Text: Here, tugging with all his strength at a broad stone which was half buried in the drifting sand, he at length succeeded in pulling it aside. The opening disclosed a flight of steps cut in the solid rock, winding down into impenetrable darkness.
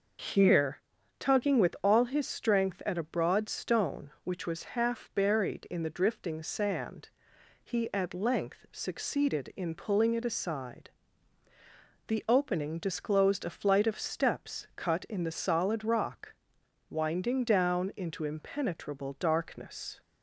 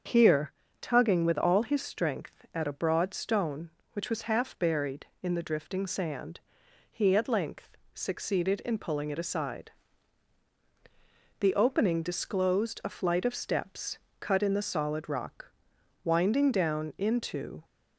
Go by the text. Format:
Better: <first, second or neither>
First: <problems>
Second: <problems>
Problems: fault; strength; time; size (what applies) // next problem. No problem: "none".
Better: first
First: none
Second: starts louder than the rest; until 1.3 s; 7 dB // pauses between "length" and "succeeded"; slight; at 7.7 s; 0.16 s long // pauses between "steps" and "cut"; slight; at 13.9 s; 0.22 s long // stops before "impenetrable darkness"; at 17.6 s